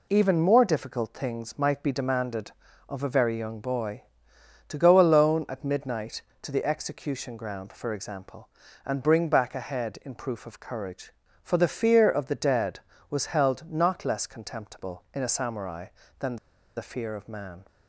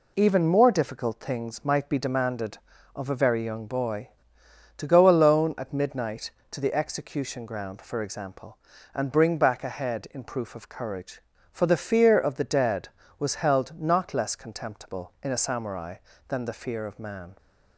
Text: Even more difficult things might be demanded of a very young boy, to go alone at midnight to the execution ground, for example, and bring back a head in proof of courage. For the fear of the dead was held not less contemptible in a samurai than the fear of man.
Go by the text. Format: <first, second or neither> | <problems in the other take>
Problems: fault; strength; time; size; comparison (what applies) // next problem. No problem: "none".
second | pauses between "than" and "the"; at 16.3 s; 0.41 s long